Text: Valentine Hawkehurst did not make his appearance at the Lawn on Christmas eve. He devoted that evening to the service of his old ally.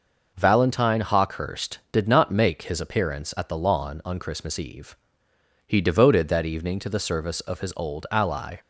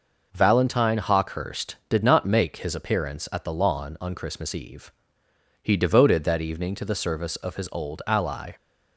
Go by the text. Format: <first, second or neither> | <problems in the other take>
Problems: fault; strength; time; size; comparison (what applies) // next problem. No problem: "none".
neither | none